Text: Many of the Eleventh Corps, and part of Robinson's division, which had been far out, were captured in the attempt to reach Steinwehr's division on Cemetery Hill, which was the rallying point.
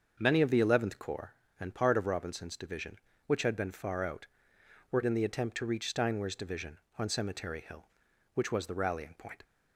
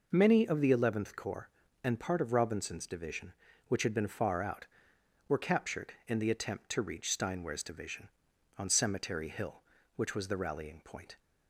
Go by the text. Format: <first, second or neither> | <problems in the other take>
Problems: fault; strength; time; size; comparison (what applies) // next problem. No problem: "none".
second | starts louder than the rest; until 1.2 s; 6.5 dB // skips "captured"; at 5.0 s